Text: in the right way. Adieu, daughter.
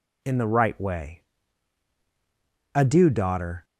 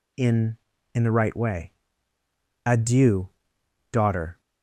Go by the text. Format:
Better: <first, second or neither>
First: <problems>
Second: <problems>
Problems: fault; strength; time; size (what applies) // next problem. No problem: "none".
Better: first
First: none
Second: says "in" twice; at 0.9 s